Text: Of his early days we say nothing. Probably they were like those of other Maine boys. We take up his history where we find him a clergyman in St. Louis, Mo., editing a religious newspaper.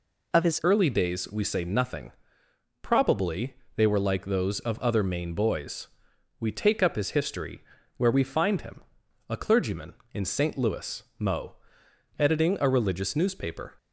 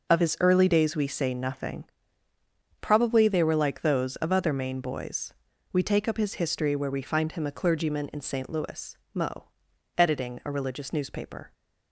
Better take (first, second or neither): second